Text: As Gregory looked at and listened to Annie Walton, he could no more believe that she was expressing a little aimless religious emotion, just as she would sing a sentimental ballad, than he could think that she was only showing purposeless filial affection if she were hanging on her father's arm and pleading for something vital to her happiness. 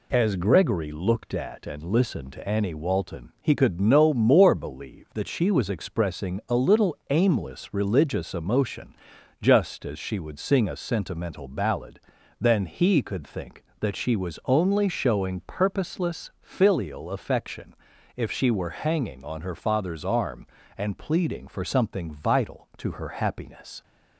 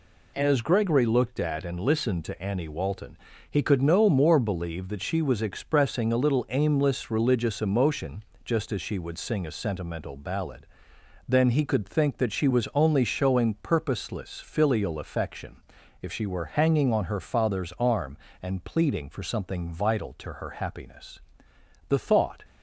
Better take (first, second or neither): first